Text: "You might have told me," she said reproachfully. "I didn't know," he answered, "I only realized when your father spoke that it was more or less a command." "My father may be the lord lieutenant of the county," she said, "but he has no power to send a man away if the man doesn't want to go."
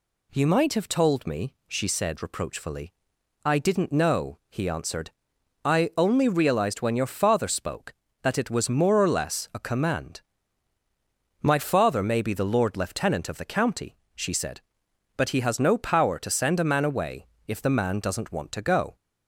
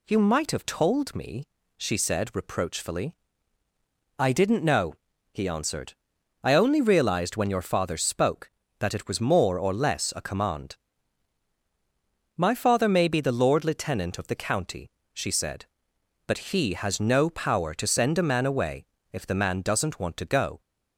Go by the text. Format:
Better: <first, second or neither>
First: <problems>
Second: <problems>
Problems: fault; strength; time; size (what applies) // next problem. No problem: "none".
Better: neither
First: pauses between "away" and "if"; slight; at 17.2 s; 0.22 s long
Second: pauses between "away" and "if"; slight; at 18.8 s; 0.26 s long